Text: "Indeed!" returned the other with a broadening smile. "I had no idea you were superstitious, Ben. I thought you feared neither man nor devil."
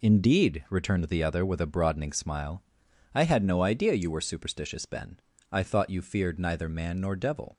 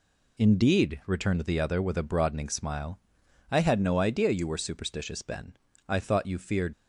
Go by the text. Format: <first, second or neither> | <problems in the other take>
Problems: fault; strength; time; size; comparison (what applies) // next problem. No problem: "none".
first | stops before "neither man nor devil"; at 6.7 s